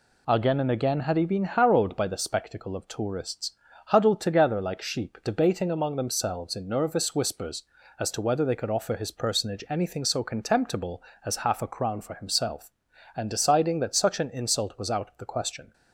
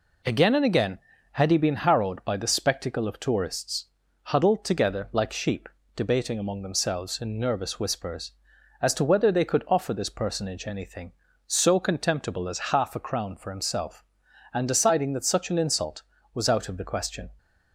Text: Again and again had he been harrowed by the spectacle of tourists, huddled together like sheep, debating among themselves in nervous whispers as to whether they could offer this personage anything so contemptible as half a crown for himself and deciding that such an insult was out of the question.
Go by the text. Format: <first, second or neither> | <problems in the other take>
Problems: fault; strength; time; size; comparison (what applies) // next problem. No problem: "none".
second | says "his" for "this"; at 8.9 s